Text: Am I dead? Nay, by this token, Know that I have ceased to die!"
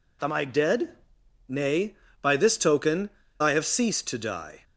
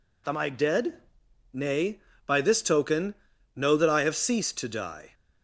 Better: second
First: skips "Know that"; at 3.2 s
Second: none

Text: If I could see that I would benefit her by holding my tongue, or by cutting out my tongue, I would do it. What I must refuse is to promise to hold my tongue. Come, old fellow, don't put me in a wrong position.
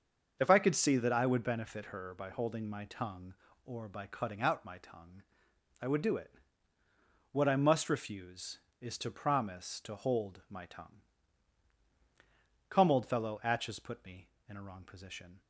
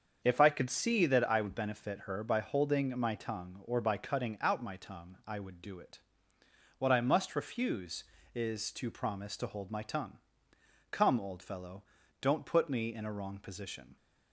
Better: second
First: starts louder than the rest; until 1.4 s; 6.5 dB // says "atches" for "don't"; at 13.4 s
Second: starts louder than the rest; until 1.2 s; 7 dB

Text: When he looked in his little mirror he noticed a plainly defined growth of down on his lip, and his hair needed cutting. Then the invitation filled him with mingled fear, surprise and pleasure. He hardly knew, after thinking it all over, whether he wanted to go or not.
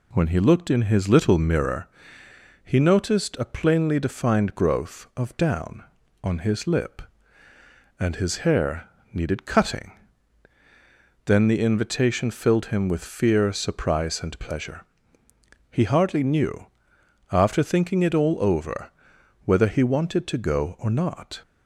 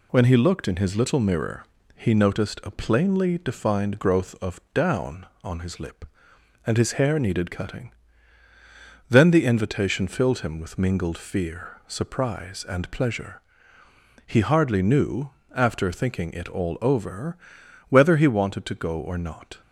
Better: second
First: pauses between "mirror" and "he"; noticeable; at 1.8 s; 0.76 s long // pauses between "hair" and "needed"; slight; at 8.8 s; 0.24 s long // skips "mingled"; at 13.0 s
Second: pauses between "mirror" and "he"; slight; at 1.6 s; 0.32 s long

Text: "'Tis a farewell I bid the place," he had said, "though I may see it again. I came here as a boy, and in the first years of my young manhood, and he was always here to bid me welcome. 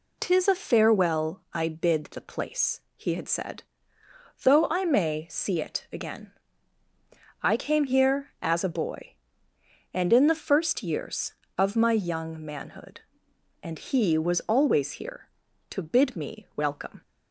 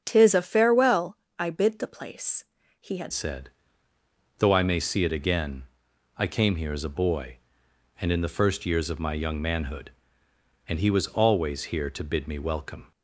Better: first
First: none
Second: starts louder than the rest; strong; until 1.0 s; 7.5 dB // pauses between "farewell" and "I"; slight; at 1.1 s; 0.22 s long // changes voice at "said"; from 3.1 s on; 9.8 s long

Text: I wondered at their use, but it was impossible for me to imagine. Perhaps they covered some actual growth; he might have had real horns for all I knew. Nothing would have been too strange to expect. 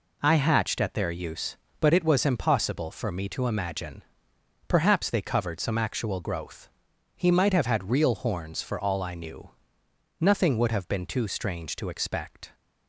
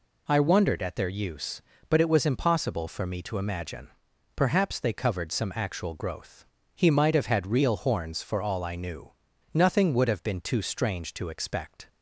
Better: second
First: says "hatched" for "wondered"; at 0.3 s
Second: none

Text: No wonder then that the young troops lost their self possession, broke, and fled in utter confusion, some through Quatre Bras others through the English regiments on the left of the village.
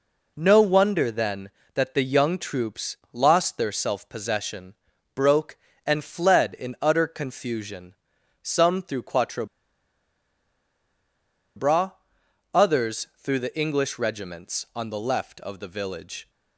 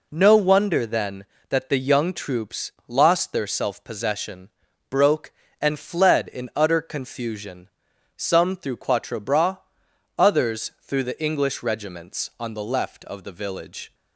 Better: second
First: pauses between "troops" and "lost"; slight; at 2.9 s; 0.16 s long // pauses between "Quatre" and "Bras"; strong; at 9.4 s; 2.1 s long // pauses between "Bras" and "others"; noticeable; at 11.9 s; 0.62 s long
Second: pauses between "troops" and "lost"; slight; at 2.7 s; 0.16 s long // pauses between "Bras" and "others"; noticeable; at 9.5 s; 0.60 s long

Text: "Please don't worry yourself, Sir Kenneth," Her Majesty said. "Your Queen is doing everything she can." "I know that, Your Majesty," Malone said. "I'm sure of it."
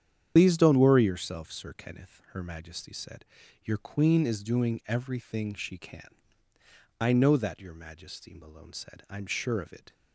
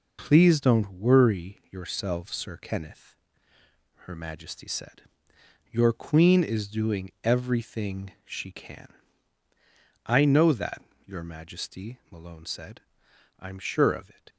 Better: second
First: loses the start of "Please"; at 0.3 s; 105 ms // starts louder than the rest; strong; until 1.3 s; 9 dB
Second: none

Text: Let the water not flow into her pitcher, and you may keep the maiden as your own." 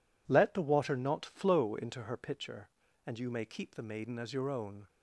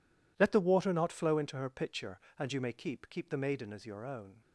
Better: first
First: none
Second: says "keep" twice; at 3.0 s

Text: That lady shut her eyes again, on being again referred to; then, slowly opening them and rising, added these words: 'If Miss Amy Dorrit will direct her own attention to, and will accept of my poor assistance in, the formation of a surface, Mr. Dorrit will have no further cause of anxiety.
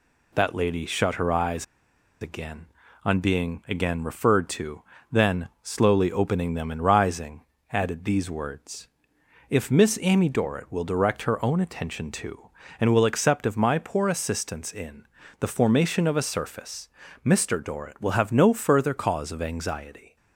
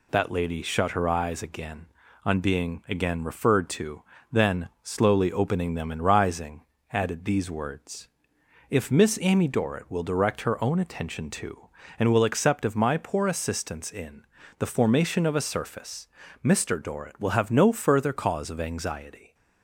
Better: second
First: pauses between "eyes" and "again"; noticeable; at 1.6 s; 0.56 s long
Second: none

